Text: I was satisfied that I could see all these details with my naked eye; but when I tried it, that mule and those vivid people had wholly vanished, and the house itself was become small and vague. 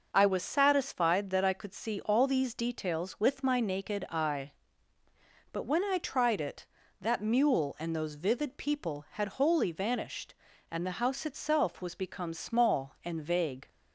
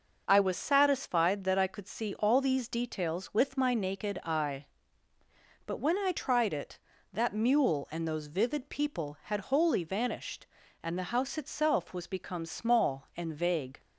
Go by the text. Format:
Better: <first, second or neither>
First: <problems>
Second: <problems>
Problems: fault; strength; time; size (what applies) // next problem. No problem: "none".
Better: neither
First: none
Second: none